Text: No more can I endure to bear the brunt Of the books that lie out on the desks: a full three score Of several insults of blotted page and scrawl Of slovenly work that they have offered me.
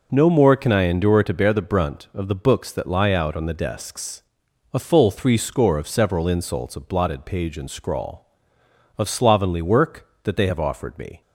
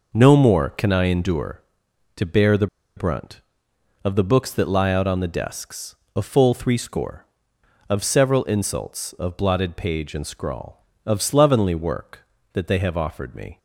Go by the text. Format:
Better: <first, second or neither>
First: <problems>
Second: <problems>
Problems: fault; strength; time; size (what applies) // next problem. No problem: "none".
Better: first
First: none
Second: pauses between "the" and "brunt"; slight; at 2.6 s; 0.30 s long